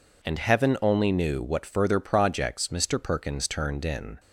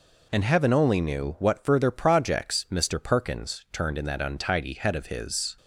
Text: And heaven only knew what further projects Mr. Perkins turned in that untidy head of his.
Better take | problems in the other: second | stops before "that untidy head of his"; at 4.1 s

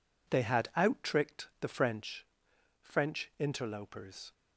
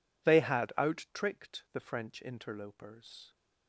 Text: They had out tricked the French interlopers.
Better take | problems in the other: second | says "French" twice; at 2.8 s

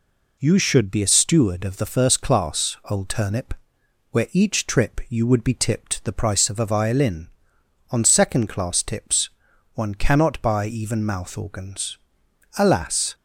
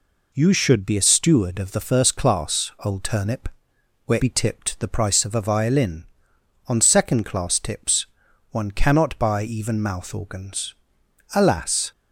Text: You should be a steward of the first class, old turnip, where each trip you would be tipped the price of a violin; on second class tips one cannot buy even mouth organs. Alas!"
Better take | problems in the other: first | skips "each trip you would"; at 4.2 s // pauses between "tips" and "one"; at 8.0 s; 0.42 s long; also in the first

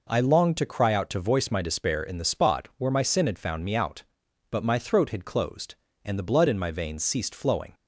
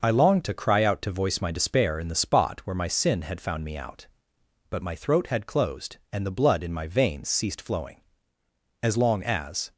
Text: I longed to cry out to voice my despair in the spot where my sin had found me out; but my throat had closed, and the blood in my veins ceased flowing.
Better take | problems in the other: first | goes on to say "As long as"; noticeable; from 8.8 s on; 0.90 s long

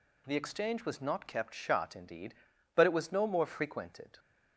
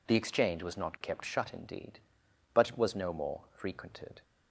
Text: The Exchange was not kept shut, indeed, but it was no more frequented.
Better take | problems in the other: neither | none

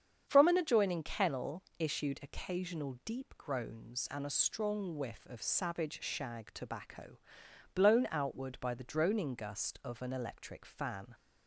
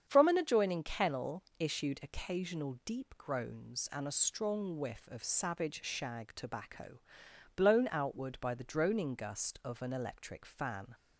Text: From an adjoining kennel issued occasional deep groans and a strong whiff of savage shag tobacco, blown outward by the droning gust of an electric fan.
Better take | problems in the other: neither | starts louder than the rest; strong; the same in both // pauses between "kennel" and "issued"; slight; the same in both

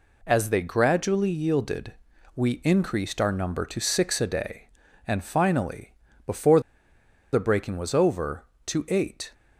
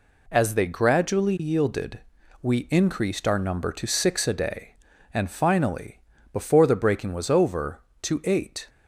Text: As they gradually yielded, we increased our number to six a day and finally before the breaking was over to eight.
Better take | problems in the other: second | pauses between "finally" and "before"; slight; at 5.9 s; 0.32 s long; slight in the second // pauses between "before" and "the"; noticeable; at 6.6 s; 0.72 s long

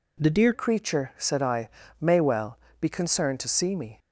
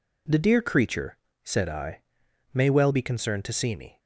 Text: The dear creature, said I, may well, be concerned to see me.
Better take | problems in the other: second | changes voice at "creature"; from 0.5 s on; 3.4 s long

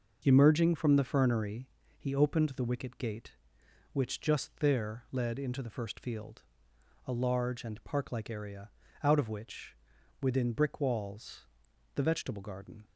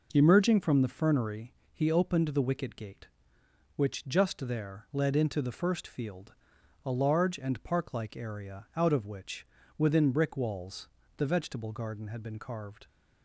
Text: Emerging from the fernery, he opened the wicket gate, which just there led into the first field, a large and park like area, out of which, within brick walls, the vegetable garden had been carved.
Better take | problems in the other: second | stops before "had been carved"; at 12.8 s

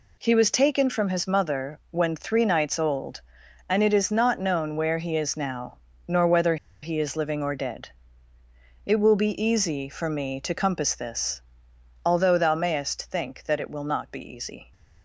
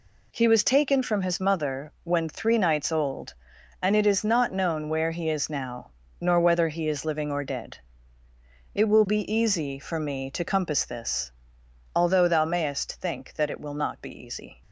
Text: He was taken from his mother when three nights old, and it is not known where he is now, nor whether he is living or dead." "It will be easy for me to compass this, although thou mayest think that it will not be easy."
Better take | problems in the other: second | pauses between "whether" and "he"; slight; at 6.5 s; 0.27 s long

